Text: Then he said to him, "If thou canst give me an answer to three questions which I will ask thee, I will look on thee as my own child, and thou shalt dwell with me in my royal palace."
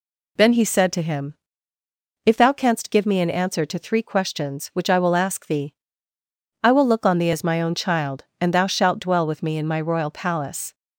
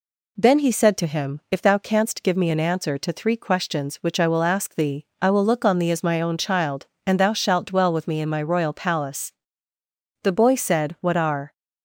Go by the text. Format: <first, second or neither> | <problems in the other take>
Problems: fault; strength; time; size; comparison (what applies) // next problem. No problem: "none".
first | goes on to say "The boy said What are"; noticeable; from 10.2 s on; 1.3 s long